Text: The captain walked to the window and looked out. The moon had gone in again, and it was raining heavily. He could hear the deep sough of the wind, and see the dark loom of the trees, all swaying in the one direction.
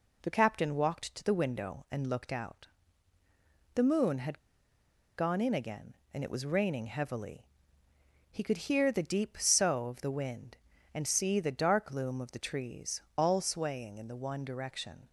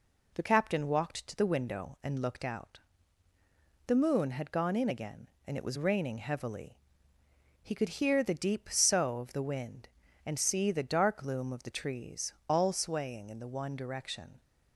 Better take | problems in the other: second | pauses between "had" and "gone"; noticeable; at 4.3 s; 0.78 s long

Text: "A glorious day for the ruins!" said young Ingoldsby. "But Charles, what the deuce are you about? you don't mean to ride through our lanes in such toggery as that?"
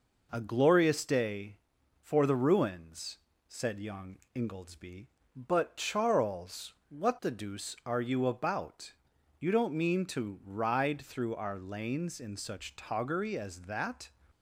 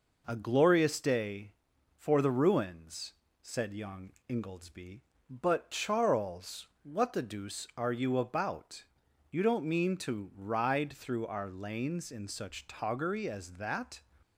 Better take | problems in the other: neither | pauses between "young" and "Ingoldsby"; slight; the same in both

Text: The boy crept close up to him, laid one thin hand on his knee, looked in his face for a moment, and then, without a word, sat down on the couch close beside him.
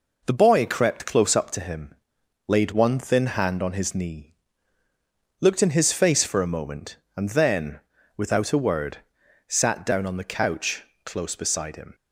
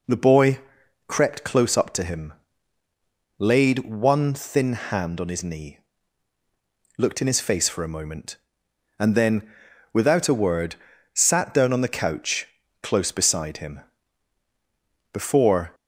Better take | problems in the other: first | pauses between "boy" and "crept"; noticeable; at 0.5 s; 0.48 s long // pauses between "couch" and "close"; slight; at 12.4 s; 0.32 s long; slight in the first // goes on to say "Before"; noticeable; from 15.1 s on; 0.62 s long

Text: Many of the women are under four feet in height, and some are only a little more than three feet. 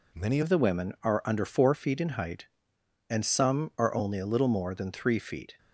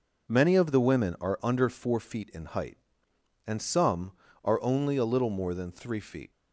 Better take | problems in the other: second | changes voice at "of"; from 0.4 s on; 5.1 s long

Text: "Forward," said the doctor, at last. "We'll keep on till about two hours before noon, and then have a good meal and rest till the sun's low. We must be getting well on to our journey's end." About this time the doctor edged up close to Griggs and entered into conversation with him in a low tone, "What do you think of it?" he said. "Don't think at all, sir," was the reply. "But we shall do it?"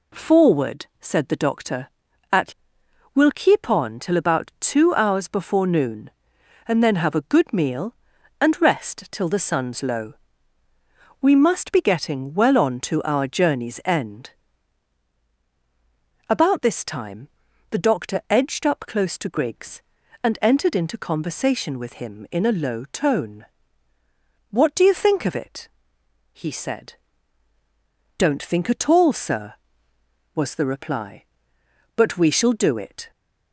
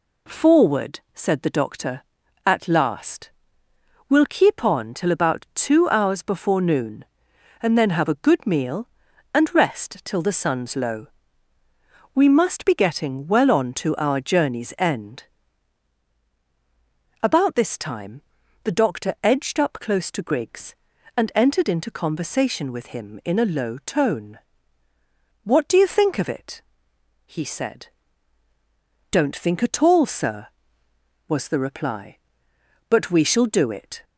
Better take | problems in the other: second | skips "last"; at 2.8 s // pauses between "time" and "the"; at 17.2 s; 0.42 s long; also in the second

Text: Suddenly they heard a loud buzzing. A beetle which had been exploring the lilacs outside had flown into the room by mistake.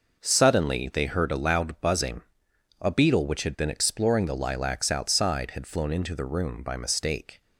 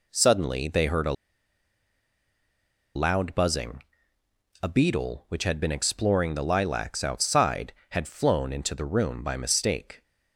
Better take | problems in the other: first | pauses between "a" and "loud"; strong; at 1.1 s; 1.8 s long

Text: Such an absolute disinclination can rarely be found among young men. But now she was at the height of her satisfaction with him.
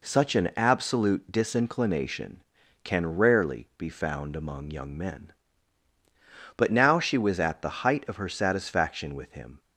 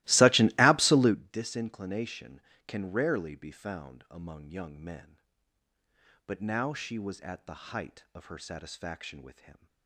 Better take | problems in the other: first | starts louder than the rest; strong; until 1.2 s; 18.5 dB

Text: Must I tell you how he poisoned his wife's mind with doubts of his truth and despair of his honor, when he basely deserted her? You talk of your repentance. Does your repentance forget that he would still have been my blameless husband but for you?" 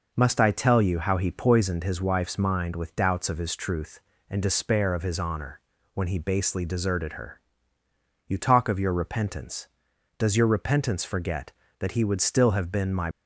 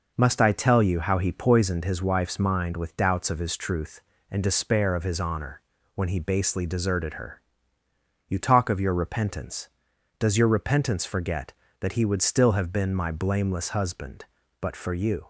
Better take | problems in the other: second | stops before "blameless husband but for you"; at 13.1 s

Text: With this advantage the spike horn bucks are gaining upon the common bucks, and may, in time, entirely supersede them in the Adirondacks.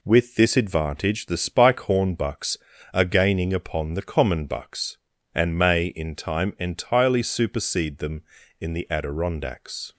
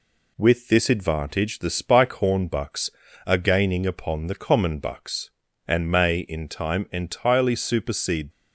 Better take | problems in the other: first | stops before "them in the Adirondacks"; at 8.3 s

